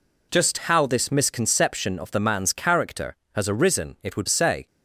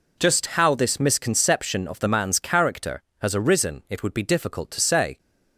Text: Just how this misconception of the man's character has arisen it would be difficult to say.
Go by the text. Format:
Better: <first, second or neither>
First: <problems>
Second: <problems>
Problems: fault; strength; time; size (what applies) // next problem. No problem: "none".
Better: second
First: skips "be difficult to"; at 4.2 s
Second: none